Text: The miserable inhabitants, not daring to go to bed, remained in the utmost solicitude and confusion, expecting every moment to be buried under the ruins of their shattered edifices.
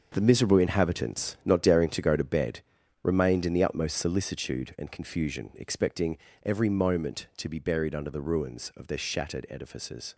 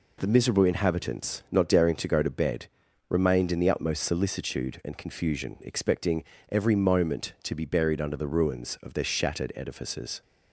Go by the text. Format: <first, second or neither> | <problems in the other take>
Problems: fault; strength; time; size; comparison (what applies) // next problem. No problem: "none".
second | gets quieter; strong; throughout; 10 dB // pauses between "expecting" and "every"; slight; at 6.1 s; 0.24 s long; slight in the second